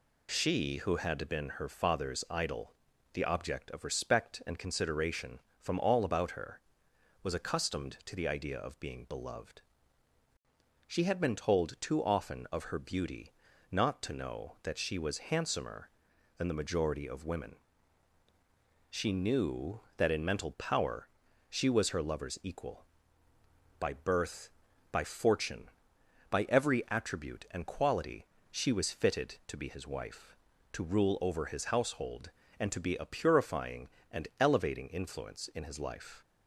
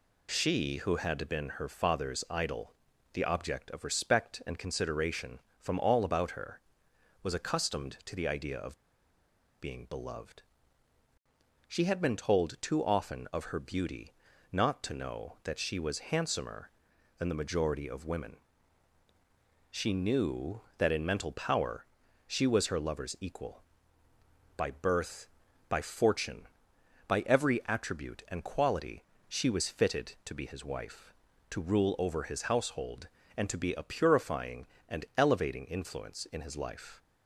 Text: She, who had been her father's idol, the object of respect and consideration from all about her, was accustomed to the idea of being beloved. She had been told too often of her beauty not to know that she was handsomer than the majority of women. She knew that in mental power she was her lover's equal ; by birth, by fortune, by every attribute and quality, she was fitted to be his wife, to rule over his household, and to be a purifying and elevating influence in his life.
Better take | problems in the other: first | pauses between "of" and "being"; noticeable; at 8.7 s; 0.81 s long // pauses between "beauty" and "not"; at 14.1 s; 0.40 s long; also in the first // pauses between "power" and "she"; at 21.8 s; 0.38 s long; also in the first

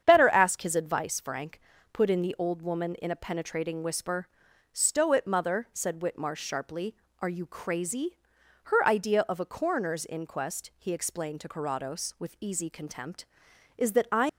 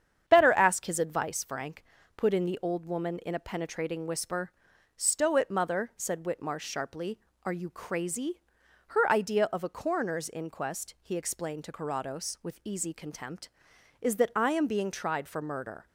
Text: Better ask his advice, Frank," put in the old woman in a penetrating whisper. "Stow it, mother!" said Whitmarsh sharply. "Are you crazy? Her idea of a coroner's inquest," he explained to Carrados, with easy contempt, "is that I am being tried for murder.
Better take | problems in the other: second | starts louder than the rest; strong; until 1.0 s; 8 dB; strong in the second // stops before "am being tried for murder"; at 14.2 s

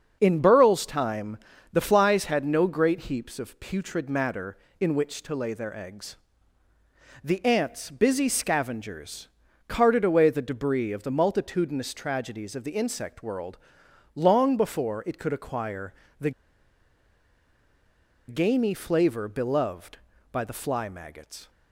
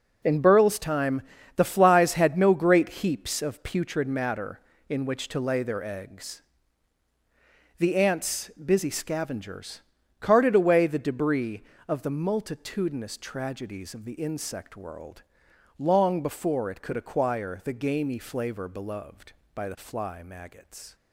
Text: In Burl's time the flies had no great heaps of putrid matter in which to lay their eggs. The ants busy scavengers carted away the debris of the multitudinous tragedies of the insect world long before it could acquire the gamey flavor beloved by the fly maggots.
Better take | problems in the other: second | starts louder than the rest; until 1.2 s; 6.5 dB // pauses between "time" and "the"; slight; at 1.3 s; 0.36 s long; slight in the second // pauses between "scavengers" and "carted"; at 9.2 s; 0.40 s long; also in the second // pauses between "world" and "long"; noticeable; at 13.5 s; 0.58 s long; noticeable in the second // pauses between "acquire" and "the"; slight; at 15.9 s; 0.28 s long // pauses between "the" and "gamey"; strong; at 16.3 s; 1.9 s long

